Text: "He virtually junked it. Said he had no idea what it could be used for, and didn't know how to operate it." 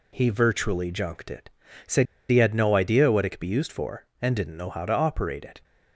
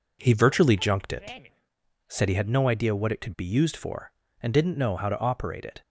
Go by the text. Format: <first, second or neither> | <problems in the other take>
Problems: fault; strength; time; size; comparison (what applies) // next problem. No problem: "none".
second | pauses between "Said" and "he"; slight; at 2.0 s; 0.23 s long